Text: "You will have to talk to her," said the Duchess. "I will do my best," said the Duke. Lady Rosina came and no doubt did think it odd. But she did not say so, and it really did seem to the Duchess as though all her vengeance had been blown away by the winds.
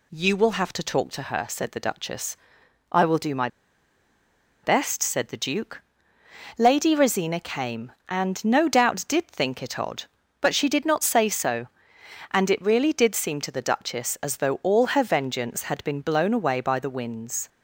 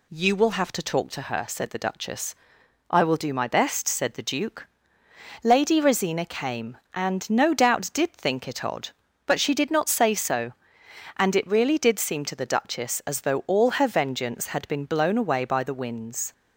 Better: second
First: pauses between "my" and "best"; at 3.4 s; 1.1 s long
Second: none

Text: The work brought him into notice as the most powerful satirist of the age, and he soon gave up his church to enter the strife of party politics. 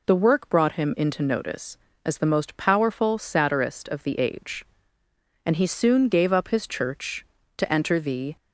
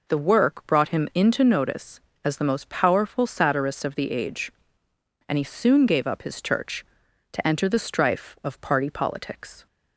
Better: second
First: stops before "strife of party politics"; at 8.3 s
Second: none

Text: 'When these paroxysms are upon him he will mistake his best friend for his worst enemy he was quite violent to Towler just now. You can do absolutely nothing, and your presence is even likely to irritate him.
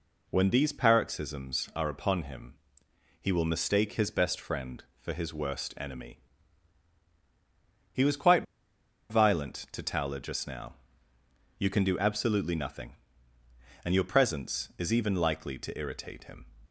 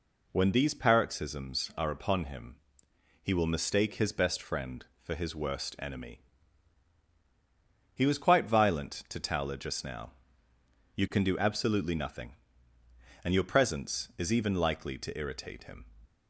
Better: second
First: pauses between "him" and "he"; noticeable; at 2.5 s; 0.64 s long // pauses between "enemy" and "he"; strong; at 6.1 s; 1.7 s long // pauses between "quite" and "violent"; noticeable; at 8.4 s; 0.66 s long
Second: pauses between "him" and "he"; noticeable; at 2.5 s; 0.64 s long // pauses between "enemy" and "he"; strong; at 6.2 s; 1.7 s long

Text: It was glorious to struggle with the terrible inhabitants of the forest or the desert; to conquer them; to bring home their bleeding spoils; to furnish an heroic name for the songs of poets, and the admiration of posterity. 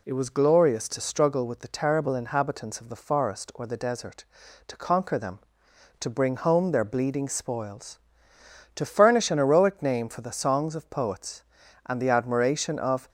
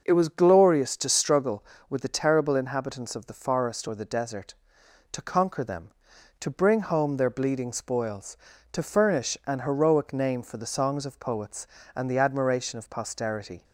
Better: second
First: stops before "posterity"; at 13.0 s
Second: none

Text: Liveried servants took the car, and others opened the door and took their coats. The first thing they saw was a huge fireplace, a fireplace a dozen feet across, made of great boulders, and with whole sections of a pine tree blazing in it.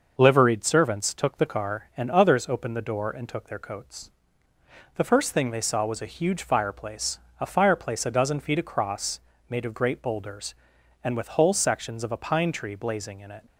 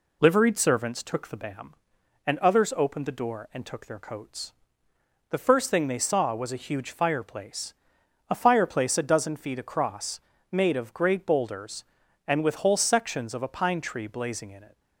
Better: first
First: none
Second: says "bam" for "car"; at 1.3 s

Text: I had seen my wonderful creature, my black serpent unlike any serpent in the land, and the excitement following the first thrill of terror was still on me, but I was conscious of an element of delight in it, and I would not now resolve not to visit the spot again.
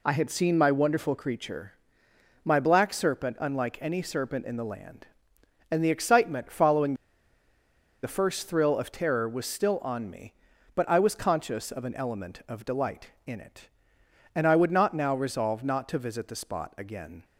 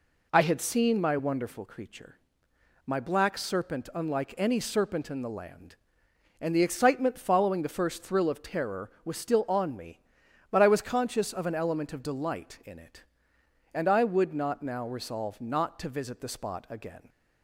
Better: second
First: pauses between "following" and "the"; at 6.9 s; 1.0 s long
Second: none

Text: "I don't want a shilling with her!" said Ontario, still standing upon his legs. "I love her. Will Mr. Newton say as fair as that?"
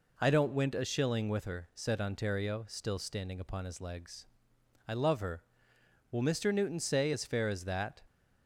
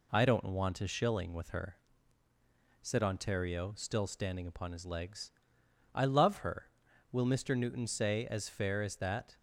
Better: second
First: says "went" for "want"; at 0.5 s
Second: none

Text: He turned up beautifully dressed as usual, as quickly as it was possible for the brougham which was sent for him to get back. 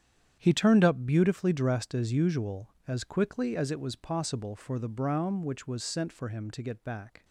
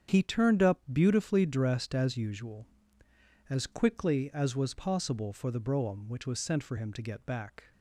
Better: first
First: starts louder than the rest; strong; until 1.4 s; 9 dB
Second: starts louder than the rest; strong; until 1.2 s; 8 dB // skips "it"; at 4.5 s

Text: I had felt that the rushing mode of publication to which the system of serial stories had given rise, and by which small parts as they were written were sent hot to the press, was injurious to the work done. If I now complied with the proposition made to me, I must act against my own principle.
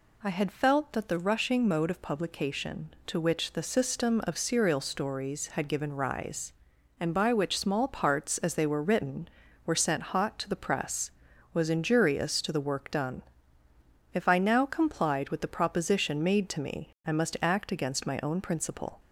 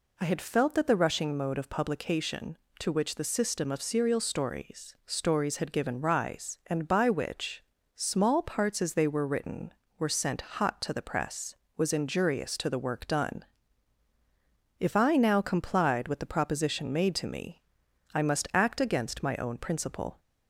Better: first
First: none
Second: says "stories" twice; at 5.0 s // pauses between "which" and "small"; slight; at 7.6 s; 0.32 s long

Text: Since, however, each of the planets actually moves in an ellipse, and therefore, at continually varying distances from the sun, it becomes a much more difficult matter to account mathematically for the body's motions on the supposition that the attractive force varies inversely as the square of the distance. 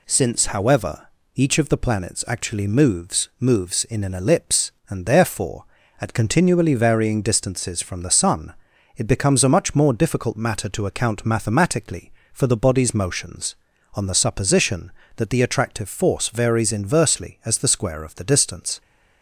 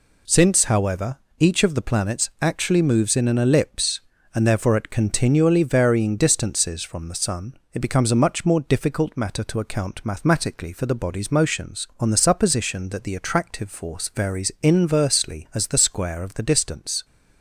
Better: second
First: says "moves" twice; at 3.4 s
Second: none

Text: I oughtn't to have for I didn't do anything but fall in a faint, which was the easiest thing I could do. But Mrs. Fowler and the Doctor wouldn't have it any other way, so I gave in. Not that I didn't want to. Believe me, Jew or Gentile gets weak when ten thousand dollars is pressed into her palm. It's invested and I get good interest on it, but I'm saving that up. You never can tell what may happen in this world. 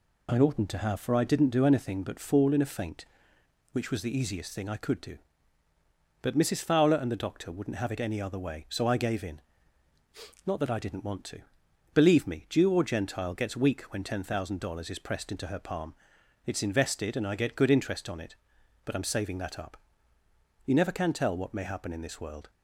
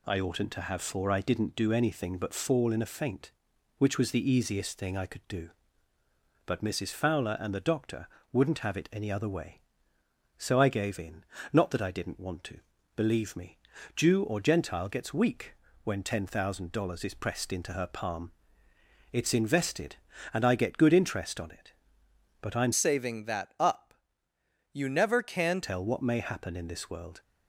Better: first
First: none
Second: pauses between "Doctor" and "wouldn't"; slight; at 8.0 s; 0.24 s long // pauses between "weak" and "when"; slight; at 15.5 s; 0.30 s long // changes voice from "saving" to "can"; from 22.7 to 25.5 s; 2.8 s long

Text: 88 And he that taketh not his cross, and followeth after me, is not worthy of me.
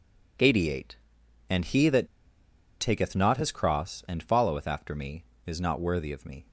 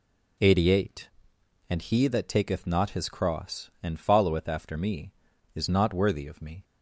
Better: second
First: pauses between "that" and "taketh"; noticeable; at 2.0 s; 0.73 s long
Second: none

